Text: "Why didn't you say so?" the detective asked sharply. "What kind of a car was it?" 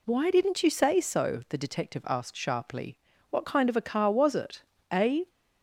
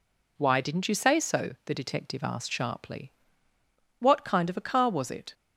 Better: second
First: goes on to say "A"; slight; from 4.9 s on; 0.36 s long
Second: none

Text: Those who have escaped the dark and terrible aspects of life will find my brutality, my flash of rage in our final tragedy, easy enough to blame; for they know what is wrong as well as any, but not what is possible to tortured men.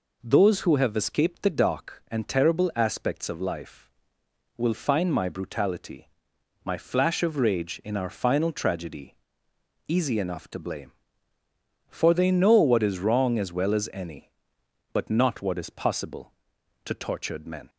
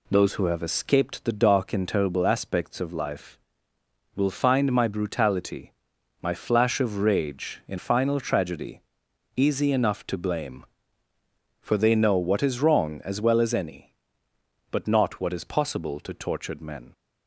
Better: first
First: none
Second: skips "our"; at 7.7 s

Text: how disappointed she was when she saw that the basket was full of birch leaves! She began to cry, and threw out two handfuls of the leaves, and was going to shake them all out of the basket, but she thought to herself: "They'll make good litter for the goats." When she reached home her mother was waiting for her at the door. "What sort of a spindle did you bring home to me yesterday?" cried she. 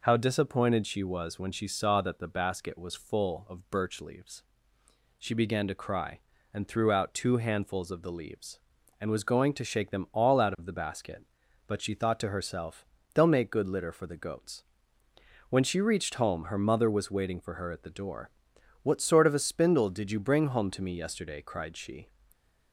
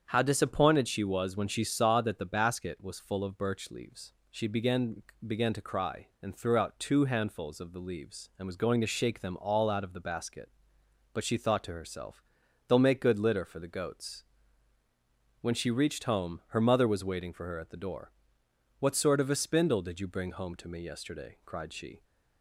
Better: first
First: none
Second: starts louder than the rest; strong; until 1.0 s; 7.5 dB // says "began" twice; at 5.2 s

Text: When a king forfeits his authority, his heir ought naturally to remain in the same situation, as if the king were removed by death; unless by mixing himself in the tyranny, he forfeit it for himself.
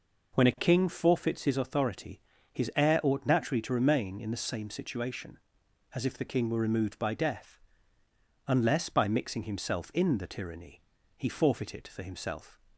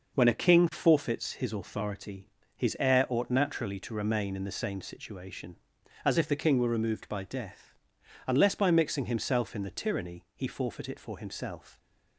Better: neither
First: none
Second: none

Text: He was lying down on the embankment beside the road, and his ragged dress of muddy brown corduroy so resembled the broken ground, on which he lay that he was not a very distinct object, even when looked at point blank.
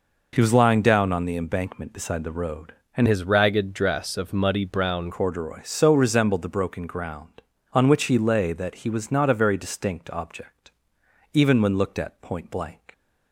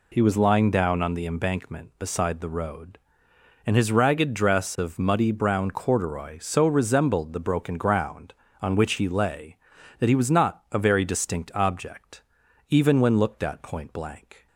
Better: second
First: changes voice from "his" to "brown"; from 3.0 to 5.1 s; 2.1 s long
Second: none

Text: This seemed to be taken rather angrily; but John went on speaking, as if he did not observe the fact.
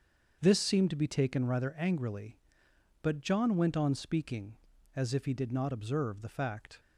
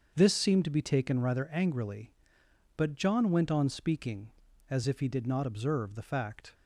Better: neither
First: starts louder than the rest; until 1.4 s; 6.5 dB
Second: starts louder than the rest; until 1.1 s; 6.5 dB

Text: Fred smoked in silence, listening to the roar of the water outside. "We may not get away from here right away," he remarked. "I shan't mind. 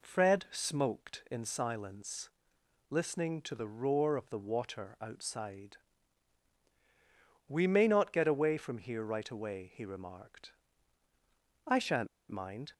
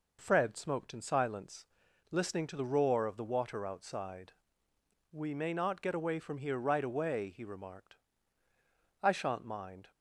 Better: second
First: pauses between "shan't" and "mind"; slight; at 12.0 s; 0.21 s long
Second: none

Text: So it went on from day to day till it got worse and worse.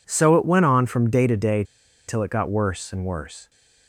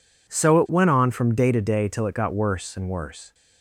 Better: second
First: pauses between "day" and "till"; at 1.6 s; 0.43 s long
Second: none

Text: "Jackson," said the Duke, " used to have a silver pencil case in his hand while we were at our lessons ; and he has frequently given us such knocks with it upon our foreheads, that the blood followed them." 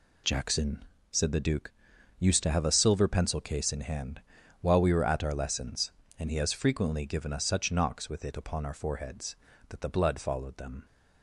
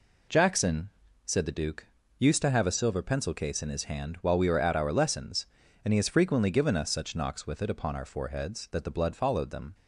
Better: second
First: skips "his"; at 3.8 s // pauses between "hand" and "while"; at 4.2 s; 0.38 s long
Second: none

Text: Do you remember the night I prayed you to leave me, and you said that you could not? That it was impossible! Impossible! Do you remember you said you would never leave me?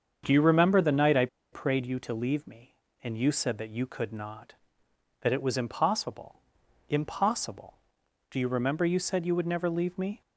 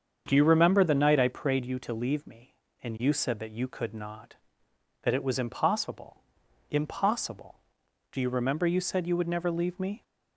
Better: second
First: starts louder than the rest; strong; until 1.2 s; 7 dB // pauses between "I" and "prayed"; slight; at 1.2 s; 0.26 s long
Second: starts louder than the rest; strong; until 1.2 s; 7 dB

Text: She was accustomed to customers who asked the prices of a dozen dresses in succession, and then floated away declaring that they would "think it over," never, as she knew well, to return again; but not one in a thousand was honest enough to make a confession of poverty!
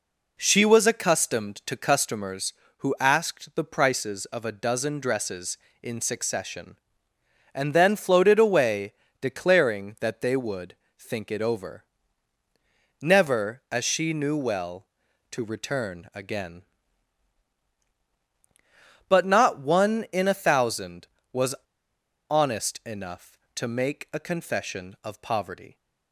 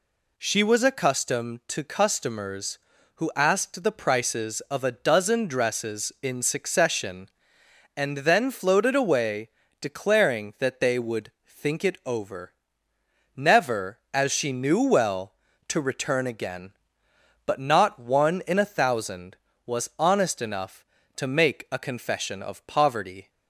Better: second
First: pauses between "away" and "declaring"; slight; at 8.9 s; 0.28 s long // pauses between "would" and "think"; slight; at 10.7 s; 0.20 s long // pauses between "was" and "honest"; noticeable; at 21.5 s; 0.78 s long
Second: pauses between "away" and "declaring"; slight; at 9.4 s; 0.30 s long // pauses between "would" and "think"; slight; at 11.3 s; 0.16 s long

